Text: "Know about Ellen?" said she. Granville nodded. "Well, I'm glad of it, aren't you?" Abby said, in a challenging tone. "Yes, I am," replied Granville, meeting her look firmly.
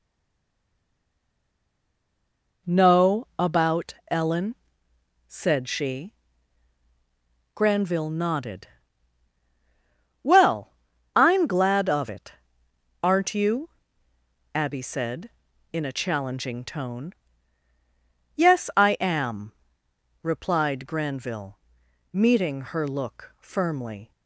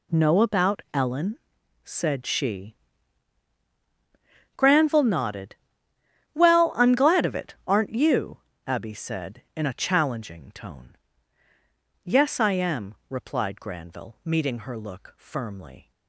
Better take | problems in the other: second | stays silent before the first word; strong; until 2.6 s; 2.6 s long // pauses between "about" and "Ellen"; slight; at 3.9 s; 0.16 s long

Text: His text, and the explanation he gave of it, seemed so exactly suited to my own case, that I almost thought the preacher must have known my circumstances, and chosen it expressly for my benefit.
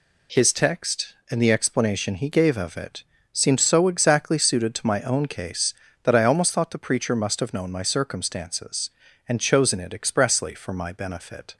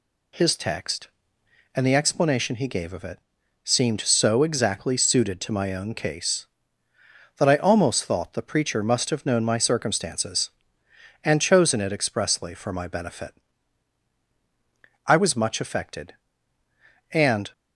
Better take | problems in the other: first | goes on to say "I was much affected and"; strong; from 15.0 s on; 2.4 s long

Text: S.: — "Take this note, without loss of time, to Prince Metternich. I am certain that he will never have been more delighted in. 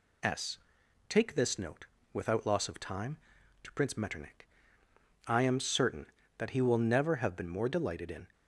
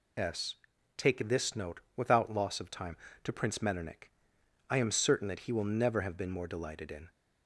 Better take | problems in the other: neither | none

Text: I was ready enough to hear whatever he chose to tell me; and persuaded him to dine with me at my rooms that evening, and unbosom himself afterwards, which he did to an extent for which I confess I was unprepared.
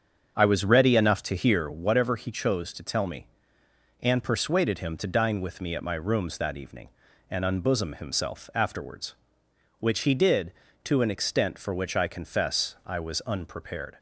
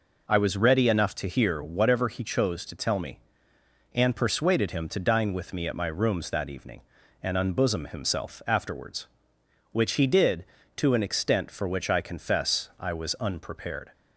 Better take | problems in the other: second | starts louder than the rest; strong; until 1.7 s; 7.5 dB

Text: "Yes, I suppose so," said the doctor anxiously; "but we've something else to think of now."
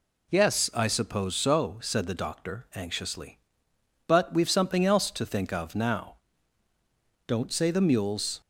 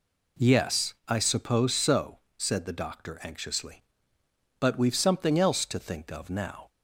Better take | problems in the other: second | goes on to say "Don't say the mules"; noticeable; from 7.2 s on; 1.1 s long

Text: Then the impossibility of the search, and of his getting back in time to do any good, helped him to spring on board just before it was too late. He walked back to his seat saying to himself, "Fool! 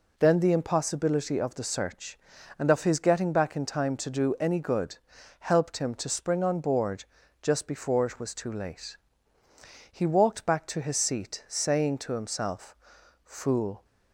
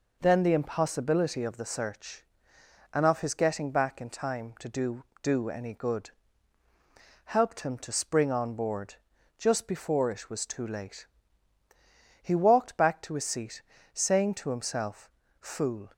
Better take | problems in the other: first | says "do" twice; at 5.2 s // pauses between "board" and "just"; at 8.9 s; 0.42 s long; also in the first // pauses between "seat" and "saying"; slight; at 13.6 s; 0.32 s long

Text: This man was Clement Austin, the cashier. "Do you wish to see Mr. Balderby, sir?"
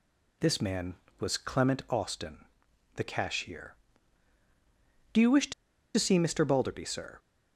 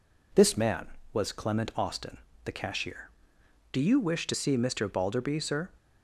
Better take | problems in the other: second | pauses between "to" and "see"; at 5.5 s; 0.44 s long

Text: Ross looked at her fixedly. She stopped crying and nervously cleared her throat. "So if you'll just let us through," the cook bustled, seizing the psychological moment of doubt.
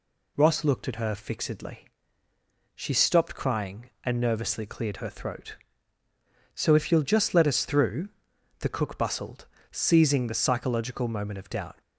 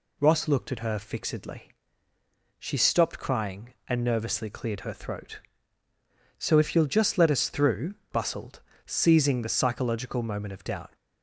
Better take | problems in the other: first | skips "the cook"; at 8.0 s

